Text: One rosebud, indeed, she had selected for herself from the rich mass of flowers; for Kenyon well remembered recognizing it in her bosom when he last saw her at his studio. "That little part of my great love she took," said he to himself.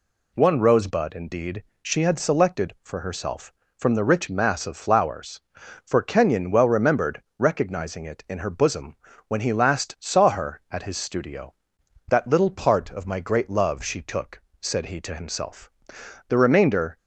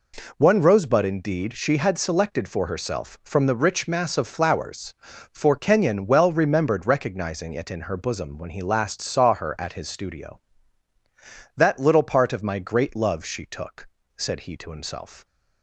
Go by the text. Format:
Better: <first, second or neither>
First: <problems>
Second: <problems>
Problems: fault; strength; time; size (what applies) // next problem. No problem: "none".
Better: second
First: pauses between "remembered" and "recognizing"; slight; at 7.2 s; 0.16 s long // pauses between "bosom" and "when"; slight; at 8.9 s; 0.32 s long // goes on to say "The remainder"; noticeable; from 16.2 s on; 0.68 s long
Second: none